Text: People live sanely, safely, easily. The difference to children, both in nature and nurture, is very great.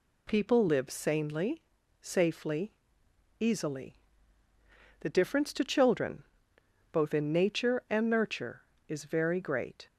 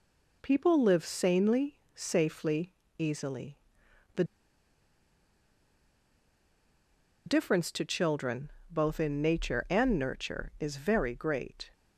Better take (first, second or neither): first